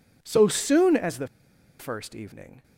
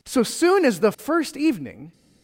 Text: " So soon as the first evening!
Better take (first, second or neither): second